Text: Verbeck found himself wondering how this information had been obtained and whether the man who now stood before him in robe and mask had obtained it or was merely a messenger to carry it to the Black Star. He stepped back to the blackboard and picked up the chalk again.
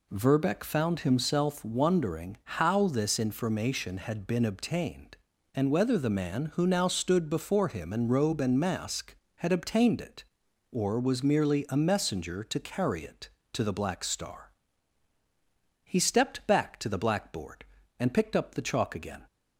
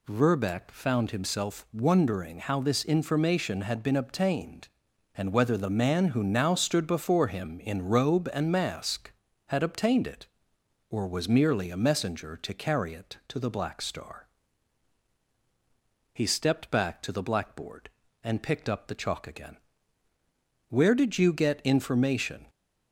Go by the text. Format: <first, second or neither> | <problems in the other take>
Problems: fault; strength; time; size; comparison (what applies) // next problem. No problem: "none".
first | goes on to say "Where did you get information"; strong; from 20.6 s on; 1.7 s long